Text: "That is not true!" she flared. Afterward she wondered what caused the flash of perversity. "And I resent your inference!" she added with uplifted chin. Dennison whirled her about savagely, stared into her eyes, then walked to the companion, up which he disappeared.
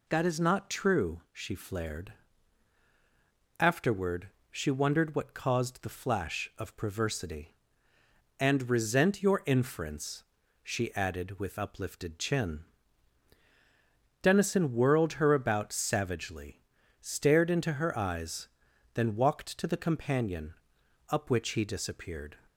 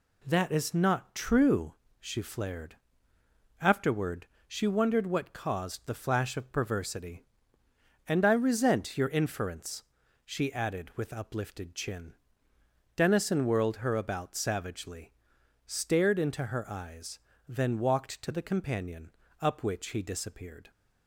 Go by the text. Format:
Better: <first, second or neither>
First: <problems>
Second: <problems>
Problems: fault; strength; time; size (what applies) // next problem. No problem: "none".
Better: second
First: pauses between "Afterward" and "she"; slight; at 4.2 s; 0.22 s long // skips "I"; at 8.6 s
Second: pauses between "Afterward" and "she"; slight; at 4.2 s; 0.20 s long